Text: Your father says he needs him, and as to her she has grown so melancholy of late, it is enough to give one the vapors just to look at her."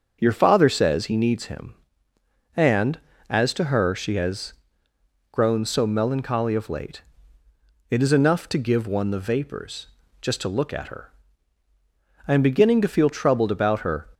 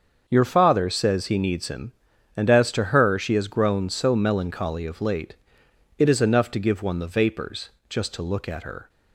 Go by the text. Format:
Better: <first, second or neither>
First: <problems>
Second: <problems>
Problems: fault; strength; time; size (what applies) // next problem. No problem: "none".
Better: second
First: starts louder than the rest; until 1.2 s; 6.5 dB // pauses between "has" and "grown"; noticeable; at 4.5 s; 0.78 s long // pauses between "vapors" and "just"; slight; at 9.8 s; 0.34 s long // goes on to say "I am beginning to feel troubled about her"; strong; from 12.2 s on; 1.8 s long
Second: starts louder than the rest; until 1.2 s; 6.5 dB // pauses between "vapors" and "just"; slight; at 7.6 s; 0.20 s long